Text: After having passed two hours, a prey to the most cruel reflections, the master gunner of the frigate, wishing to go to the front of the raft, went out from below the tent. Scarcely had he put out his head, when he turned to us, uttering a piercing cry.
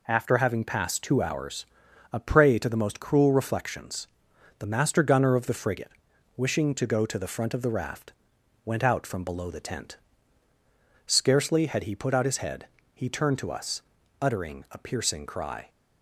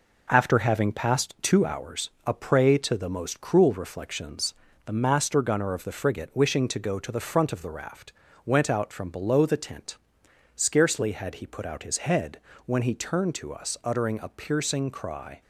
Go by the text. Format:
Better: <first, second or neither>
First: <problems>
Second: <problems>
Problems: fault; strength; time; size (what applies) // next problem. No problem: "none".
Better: second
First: skips "when"; at 12.8 s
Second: none